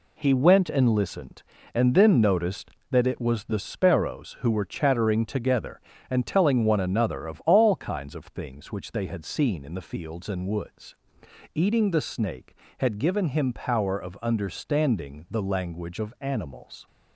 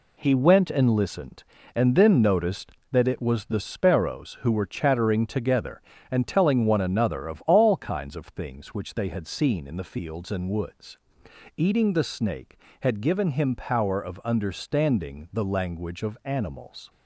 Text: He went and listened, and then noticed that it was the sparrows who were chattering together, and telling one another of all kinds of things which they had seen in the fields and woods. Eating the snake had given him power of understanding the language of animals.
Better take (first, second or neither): neither